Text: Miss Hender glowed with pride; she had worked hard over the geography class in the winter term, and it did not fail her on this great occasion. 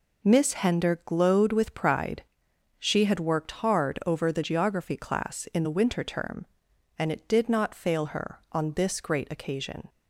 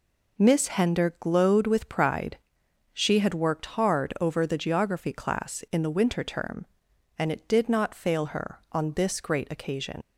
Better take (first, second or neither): first